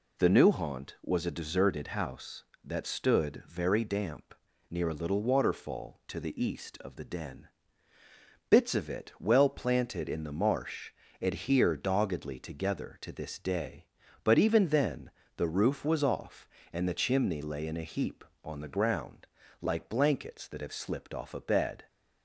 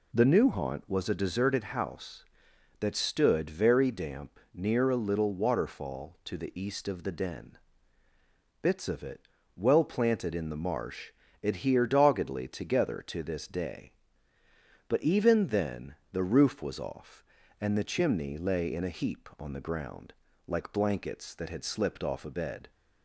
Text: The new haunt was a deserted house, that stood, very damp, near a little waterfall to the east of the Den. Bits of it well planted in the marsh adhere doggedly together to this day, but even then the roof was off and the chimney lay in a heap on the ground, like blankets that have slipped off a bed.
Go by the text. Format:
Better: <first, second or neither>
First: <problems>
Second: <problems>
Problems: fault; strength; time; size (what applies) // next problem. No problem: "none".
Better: first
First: pauses between "marsh" and "adhere"; slight; at 10.9 s; 0.28 s long // pauses between "then" and "the"; slight; at 15.1 s; 0.24 s long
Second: pauses between "it" and "well"; slight; at 9.2 s; 0.34 s long // pauses between "marsh" and "adhere"; slight; at 11.1 s; 0.32 s long // pauses between "then" and "the"; slight; at 15.9 s; 0.18 s long // says "had" for "have"; at 21.5 s